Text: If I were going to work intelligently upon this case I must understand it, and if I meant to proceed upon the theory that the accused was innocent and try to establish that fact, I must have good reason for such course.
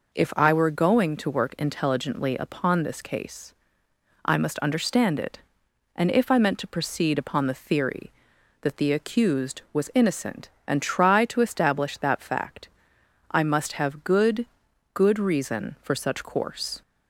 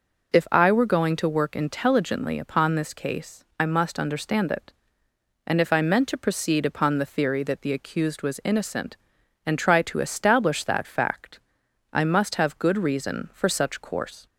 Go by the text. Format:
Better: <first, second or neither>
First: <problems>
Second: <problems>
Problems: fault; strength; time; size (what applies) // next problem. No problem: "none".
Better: second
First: pauses between "case" and "I"; noticeable; at 3.5 s; 0.72 s long // says "good" twice; at 14.9 s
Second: pauses between "case" and "I"; slight; at 3.4 s; 0.16 s long